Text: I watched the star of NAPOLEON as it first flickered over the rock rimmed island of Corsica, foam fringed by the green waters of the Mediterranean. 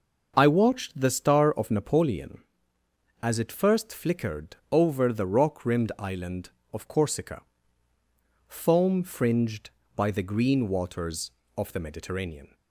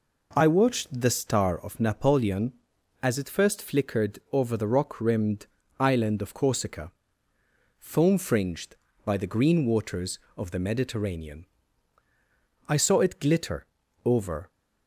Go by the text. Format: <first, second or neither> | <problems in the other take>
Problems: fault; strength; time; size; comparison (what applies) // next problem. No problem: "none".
first | pauses between "rimmed" and "island"; slight; at 5.4 s; 0.32 s long // goes on to say "I saw it glitter over"; strong; from 12.6 s on; 1.8 s long